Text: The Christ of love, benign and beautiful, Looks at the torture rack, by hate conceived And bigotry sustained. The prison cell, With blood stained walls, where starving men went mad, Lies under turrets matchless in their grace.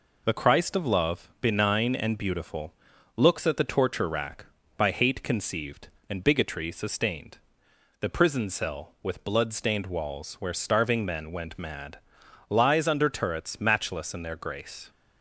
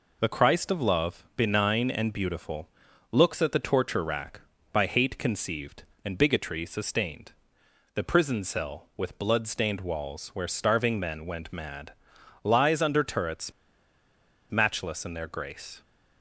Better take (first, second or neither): first